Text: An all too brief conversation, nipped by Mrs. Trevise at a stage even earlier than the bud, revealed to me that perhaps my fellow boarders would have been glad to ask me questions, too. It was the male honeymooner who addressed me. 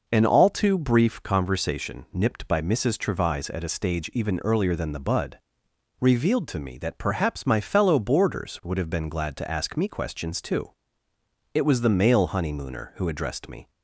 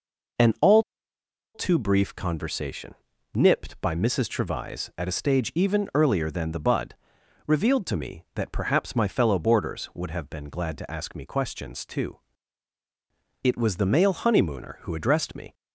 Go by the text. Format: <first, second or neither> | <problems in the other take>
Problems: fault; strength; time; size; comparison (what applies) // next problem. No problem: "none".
first | pauses between "all" and "too"; noticeable; at 0.8 s; 0.72 s long